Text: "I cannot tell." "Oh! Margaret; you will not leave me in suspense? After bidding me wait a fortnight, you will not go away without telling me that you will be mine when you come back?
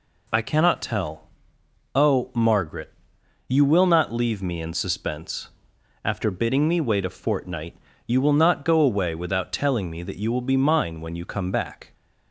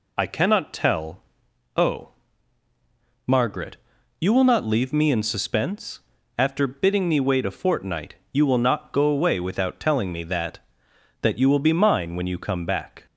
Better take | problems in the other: first | says "that" twice; at 11.2 s

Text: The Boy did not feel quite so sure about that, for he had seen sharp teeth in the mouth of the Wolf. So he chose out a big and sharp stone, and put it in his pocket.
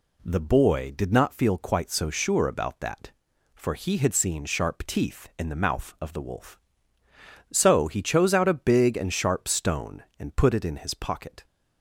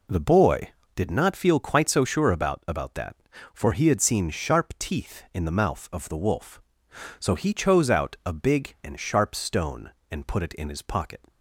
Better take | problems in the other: first | says "about" twice; at 2.6 s

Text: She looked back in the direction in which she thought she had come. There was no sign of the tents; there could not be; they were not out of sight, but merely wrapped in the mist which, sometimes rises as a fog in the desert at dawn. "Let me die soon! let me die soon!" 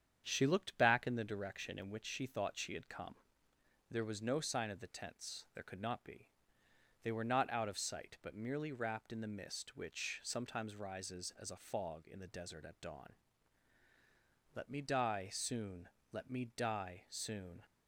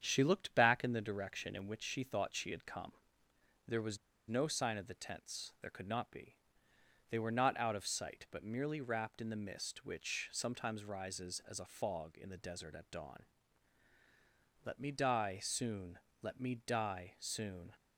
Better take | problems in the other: first | starts louder than the rest; strong; until 1.0 s; 8 dB; strong in the first // pauses between "was" and "no"; slight; at 3.9 s; 0.32 s long

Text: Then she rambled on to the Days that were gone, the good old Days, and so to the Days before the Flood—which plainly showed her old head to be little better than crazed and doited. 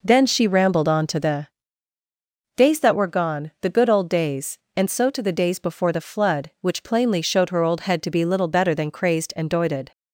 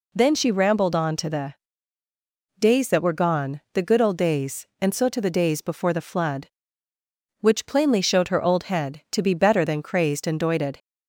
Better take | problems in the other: first | pauses between "the" and "Days"; at 1.5 s; 1.0 s long; also in the first // skips "little"; at 9.3 s

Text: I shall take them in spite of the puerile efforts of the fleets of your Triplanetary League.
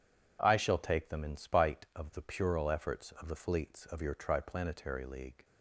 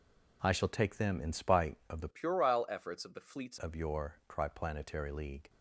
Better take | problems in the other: first | changes voice from "puerile" to "fleets"; from 2.1 to 3.5 s; 1.4 s long

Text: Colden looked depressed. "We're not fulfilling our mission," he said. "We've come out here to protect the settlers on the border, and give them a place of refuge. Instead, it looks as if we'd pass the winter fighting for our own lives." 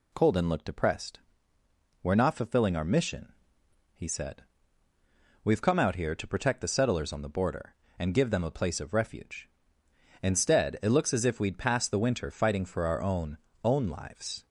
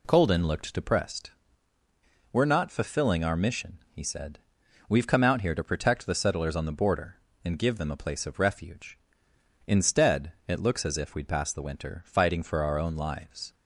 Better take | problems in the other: second | says "own" twice; at 13.6 s

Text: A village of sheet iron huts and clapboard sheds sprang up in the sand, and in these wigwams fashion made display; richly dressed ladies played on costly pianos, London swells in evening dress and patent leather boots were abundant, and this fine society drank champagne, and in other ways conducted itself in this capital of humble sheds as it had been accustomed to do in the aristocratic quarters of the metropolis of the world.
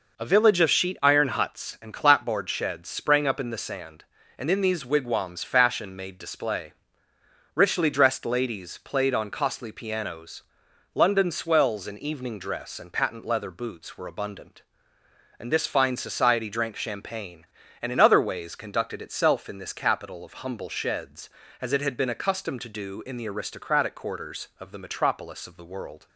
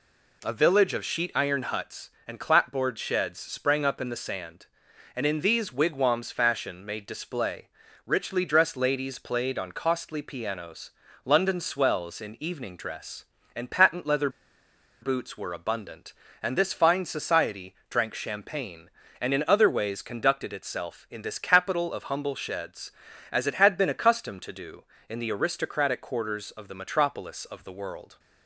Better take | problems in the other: first | pauses between "leather" and "boots"; noticeable; at 14.2 s; 0.73 s long // pauses between "society" and "drank"; slight; at 17.7 s; 0.16 s long

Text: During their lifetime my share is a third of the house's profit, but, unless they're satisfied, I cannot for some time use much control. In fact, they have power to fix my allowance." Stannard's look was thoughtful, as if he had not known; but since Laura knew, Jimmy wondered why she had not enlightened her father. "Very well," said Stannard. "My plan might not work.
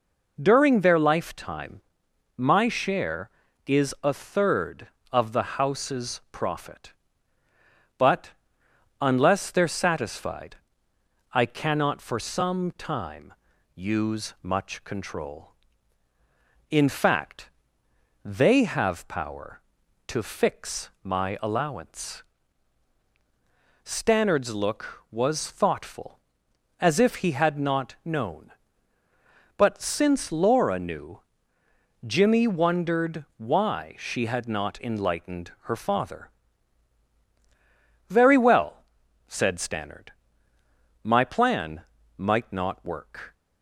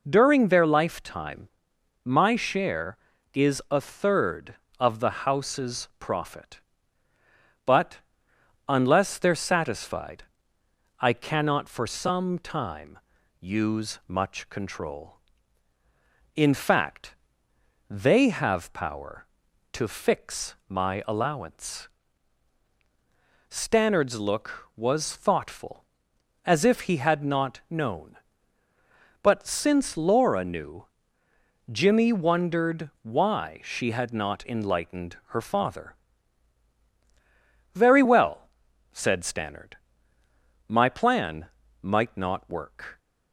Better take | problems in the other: neither | pauses between "lifetime" and "my"; noticeable; the same in both // pauses between "time" and "use"; the same in both // pauses between "plan" and "might"; slight; the same in both

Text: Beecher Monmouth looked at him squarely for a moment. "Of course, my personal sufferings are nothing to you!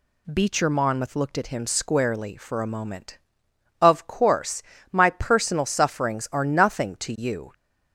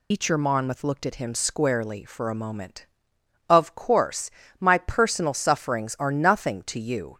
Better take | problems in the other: first | loses the start of "Beecher"; at 0.1 s; 155 ms

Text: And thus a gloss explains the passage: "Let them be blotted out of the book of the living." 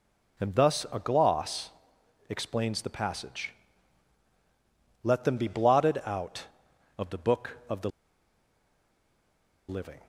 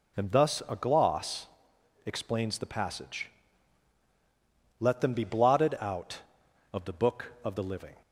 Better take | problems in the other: second | pauses between "gloss" and "explains"; noticeable; at 1.7 s; 0.58 s long; noticeable in the second // pauses between "the" and "living"; strong; at 7.8 s; 1.7 s long

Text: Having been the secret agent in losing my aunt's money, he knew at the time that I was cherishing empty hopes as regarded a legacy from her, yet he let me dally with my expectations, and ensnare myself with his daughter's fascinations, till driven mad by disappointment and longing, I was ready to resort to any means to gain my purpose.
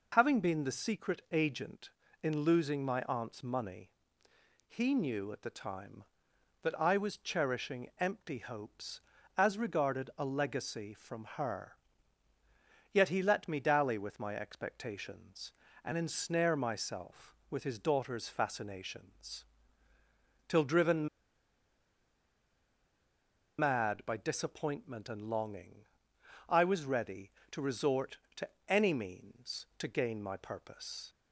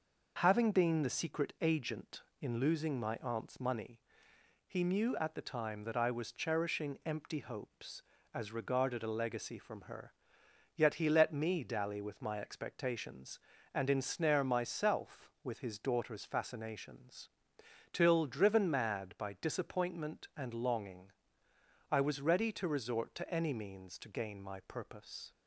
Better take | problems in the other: second | pauses between "driven" and "mad"; strong; at 21.0 s; 2.5 s long // pauses between "to" and "any"; slight; at 28.4 s; 0.22 s long

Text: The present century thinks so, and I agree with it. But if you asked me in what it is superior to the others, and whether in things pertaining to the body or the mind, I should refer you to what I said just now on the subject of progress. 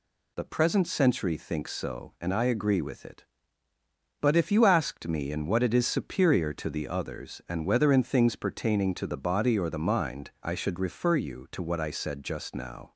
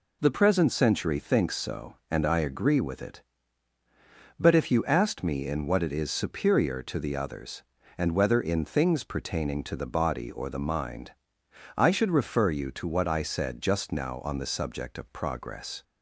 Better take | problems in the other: second | stops before "on the subject of progress"; at 12.9 s

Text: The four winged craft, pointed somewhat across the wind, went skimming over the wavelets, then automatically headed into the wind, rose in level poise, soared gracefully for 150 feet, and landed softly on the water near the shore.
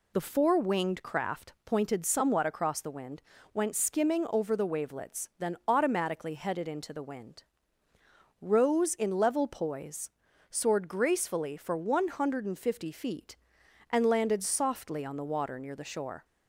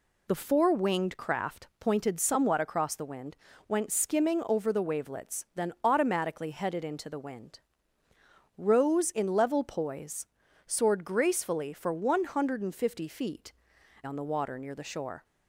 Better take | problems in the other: first | skips "and landed softly"; at 13.7 s

